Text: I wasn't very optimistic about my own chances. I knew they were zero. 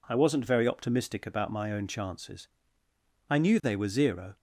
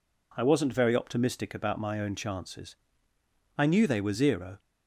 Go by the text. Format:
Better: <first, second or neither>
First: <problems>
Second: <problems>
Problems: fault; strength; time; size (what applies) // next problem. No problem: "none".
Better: neither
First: none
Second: none